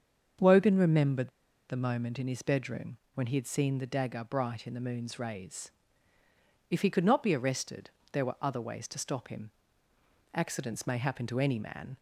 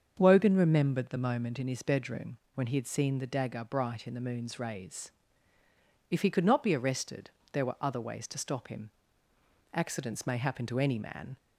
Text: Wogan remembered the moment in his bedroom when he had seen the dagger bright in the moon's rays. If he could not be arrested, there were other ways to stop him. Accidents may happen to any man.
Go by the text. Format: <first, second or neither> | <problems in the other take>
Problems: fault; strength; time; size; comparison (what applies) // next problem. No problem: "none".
second | starts louder than the rest; until 1.8 s; 7 dB; also in the second // pauses between "remembered" and "the"; at 1.3 s; 0.37 s long // pauses between "bedroom" and "when"; slight; at 2.9 s; 0.18 s long; slight in the second